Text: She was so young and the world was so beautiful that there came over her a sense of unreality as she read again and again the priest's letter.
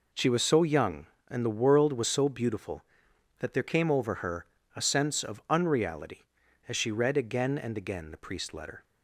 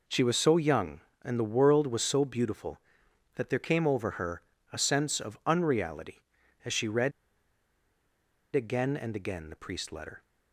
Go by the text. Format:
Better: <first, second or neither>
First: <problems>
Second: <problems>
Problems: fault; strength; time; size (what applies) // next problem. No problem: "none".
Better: first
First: pauses between "her" and "a"; slight; at 4.4 s; 0.29 s long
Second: pauses between "her" and "a"; slight; at 4.4 s; 0.30 s long // pauses between "read" and "again"; strong; at 7.1 s; 1.4 s long